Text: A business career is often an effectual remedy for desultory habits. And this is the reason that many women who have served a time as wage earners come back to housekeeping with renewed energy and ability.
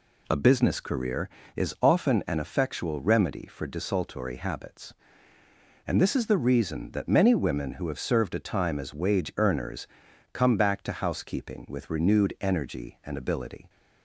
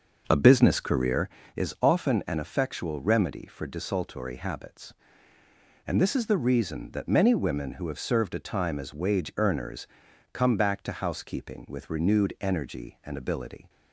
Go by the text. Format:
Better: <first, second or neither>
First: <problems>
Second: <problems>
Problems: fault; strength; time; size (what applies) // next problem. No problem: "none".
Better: first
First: pauses between "earners" and "come"; noticeable; at 9.8 s; 0.46 s long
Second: starts louder than the rest; noticeable; until 1.3 s; 6 dB // pauses between "earners" and "come"; noticeable; at 9.8 s; 0.46 s long